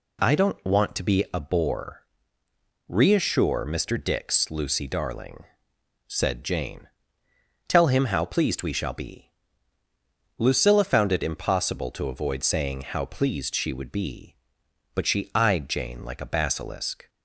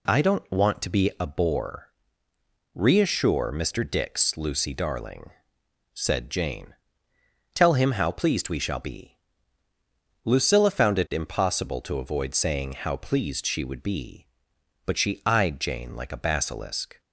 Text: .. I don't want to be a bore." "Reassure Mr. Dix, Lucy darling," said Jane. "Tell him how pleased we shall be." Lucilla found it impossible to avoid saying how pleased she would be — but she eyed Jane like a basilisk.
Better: neither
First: none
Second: none

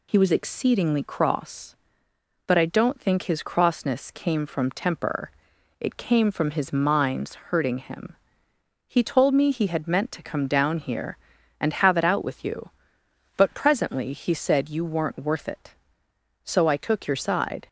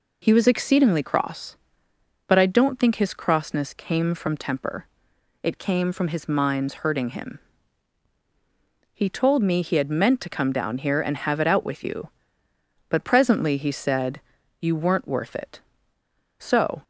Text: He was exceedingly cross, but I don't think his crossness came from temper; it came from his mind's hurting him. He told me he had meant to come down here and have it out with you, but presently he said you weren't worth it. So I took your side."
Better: first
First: none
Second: pauses between "said" and "you"; at 14.2 s; 0.40 s long // stops before "I took your side"; at 16.8 s

